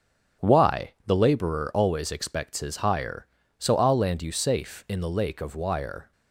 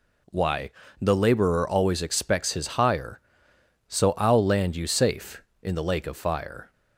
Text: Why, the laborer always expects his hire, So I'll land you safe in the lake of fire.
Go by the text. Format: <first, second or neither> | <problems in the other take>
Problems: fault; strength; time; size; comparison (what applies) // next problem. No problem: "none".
second | starts louder than the rest; strong; until 1.5 s; 7 dB // says "wire" for "fire"; at 5.5 s